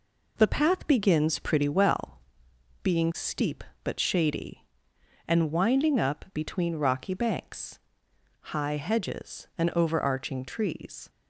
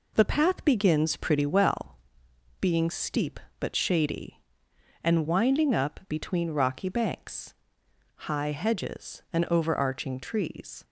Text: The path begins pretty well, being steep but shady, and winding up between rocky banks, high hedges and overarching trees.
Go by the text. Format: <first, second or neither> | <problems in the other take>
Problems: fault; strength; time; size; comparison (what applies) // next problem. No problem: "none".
neither | none